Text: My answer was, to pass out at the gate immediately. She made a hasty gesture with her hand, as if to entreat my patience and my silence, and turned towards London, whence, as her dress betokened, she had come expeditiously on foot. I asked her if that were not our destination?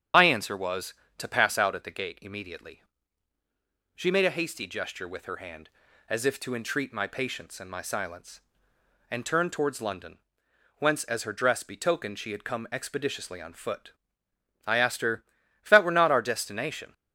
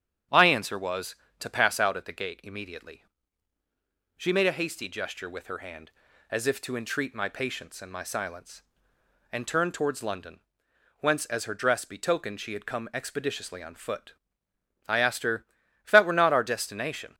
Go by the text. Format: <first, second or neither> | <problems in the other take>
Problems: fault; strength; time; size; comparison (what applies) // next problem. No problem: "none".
second | loses the start of "My"; at 0.1 s; 55 ms // starts louder than the rest; strong; until 1.3 s; 8.5 dB; strong in the second // pauses between "her" and "if"; at 15.2 s; 0.40 s long; also in the second